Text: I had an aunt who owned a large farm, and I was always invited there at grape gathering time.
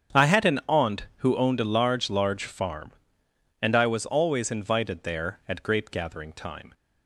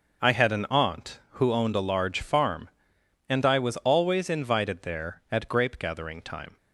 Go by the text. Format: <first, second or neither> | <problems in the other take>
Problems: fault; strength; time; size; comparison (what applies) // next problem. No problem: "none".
second | starts louder than the rest; strong; until 1.3 s; 8 dB // says "large" twice; at 2.0 s